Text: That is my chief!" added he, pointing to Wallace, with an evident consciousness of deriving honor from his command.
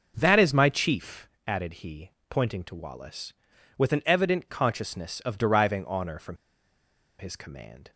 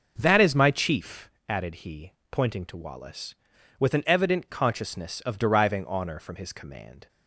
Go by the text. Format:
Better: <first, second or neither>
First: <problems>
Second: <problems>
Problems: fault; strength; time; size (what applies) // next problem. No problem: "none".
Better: second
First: pauses between "from" and "his"; noticeable; at 6.3 s; 0.83 s long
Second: none